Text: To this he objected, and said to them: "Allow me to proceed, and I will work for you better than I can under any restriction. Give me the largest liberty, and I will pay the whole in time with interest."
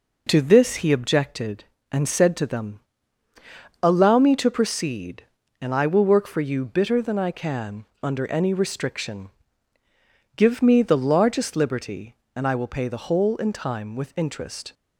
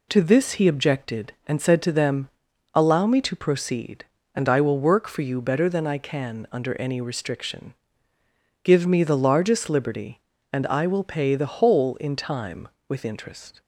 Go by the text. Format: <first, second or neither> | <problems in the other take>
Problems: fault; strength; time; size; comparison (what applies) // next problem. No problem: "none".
second | says "bitter" for "better"; at 6.6 s // pauses between "can" and "under"; slight; at 7.8 s; 0.18 s long